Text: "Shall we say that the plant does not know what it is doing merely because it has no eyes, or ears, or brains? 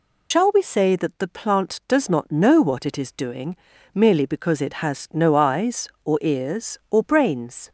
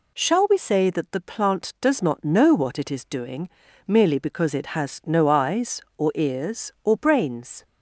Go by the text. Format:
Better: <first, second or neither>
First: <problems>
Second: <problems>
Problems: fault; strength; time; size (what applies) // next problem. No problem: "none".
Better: second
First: loses the start of "Shall"; at 0.3 s; 110 ms // pauses between "doing" and "merely"; at 3.5 s; 0.38 s long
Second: pauses between "doing" and "merely"; at 3.4 s; 0.38 s long